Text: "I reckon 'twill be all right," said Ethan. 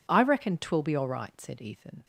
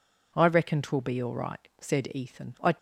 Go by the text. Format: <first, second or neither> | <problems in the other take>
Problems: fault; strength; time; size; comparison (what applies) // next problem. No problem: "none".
first | goes on to say "I"; slight; from 2.6 s on; 0.12 s long